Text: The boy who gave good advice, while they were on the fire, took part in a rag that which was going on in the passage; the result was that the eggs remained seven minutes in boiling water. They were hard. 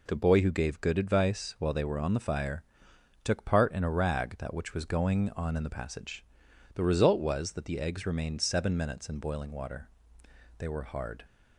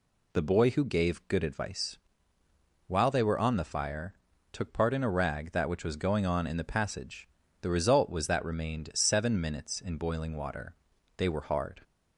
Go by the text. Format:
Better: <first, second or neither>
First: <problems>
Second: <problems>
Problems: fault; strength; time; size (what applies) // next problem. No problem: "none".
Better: first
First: none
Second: skips "the eggs"; at 8.4 s